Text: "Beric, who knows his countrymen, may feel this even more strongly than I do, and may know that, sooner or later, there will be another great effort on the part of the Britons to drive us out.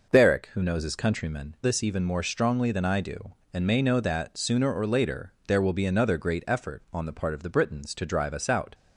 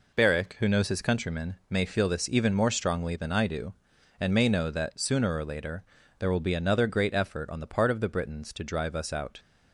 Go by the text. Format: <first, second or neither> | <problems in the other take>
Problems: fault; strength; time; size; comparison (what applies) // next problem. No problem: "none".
second | skips "may feel"; at 1.5 s